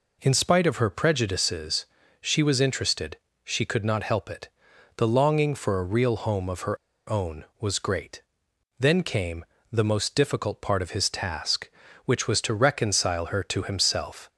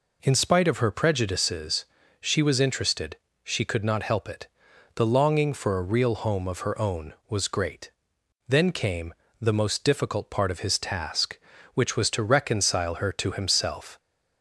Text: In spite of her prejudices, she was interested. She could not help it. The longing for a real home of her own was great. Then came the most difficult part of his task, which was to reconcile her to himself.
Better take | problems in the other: second | pauses between "her" and "own"; slight; at 6.7 s; 0.35 s long // pauses between "came" and "the"; slight; at 9.4 s; 0.26 s long; slight in the second

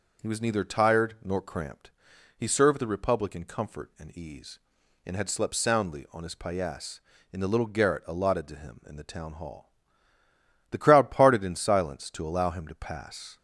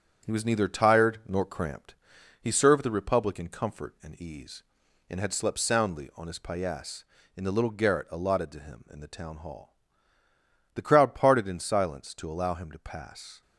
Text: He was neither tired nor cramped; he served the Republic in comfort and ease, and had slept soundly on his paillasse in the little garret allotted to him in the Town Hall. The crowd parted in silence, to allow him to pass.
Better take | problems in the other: first | gets quieter; noticeable; throughout; 4.5 dB

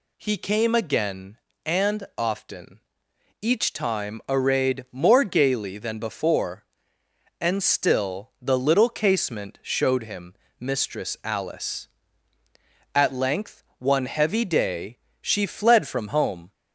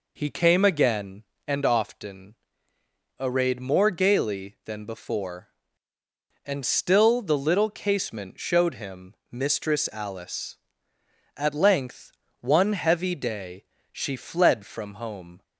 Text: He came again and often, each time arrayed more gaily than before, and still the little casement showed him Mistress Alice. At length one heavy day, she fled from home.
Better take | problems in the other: first | skips "each time"; at 2.7 s // pauses between "him" and "Mistress"; slight; at 9.1 s; 0.16 s long; slight in the first // pauses between "length" and "one"; slight; at 12.0 s; 0.30 s long; slight in the first

